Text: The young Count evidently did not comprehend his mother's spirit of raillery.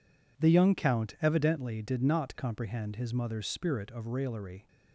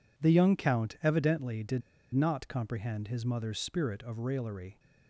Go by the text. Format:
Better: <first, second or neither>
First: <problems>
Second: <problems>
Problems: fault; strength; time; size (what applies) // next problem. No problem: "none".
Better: first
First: none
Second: pauses between "did" and "not"; slight; at 1.8 s; 0.34 s long